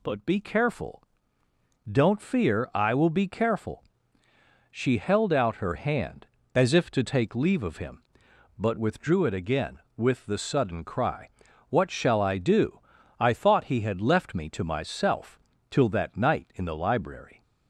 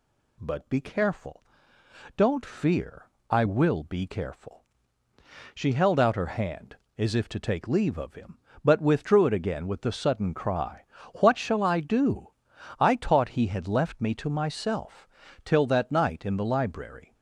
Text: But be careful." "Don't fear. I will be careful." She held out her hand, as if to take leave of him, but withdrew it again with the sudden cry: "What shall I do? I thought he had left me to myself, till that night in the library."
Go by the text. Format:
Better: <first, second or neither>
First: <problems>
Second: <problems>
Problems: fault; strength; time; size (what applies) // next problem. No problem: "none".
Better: first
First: none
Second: says "taught" for "thought"; at 12.9 s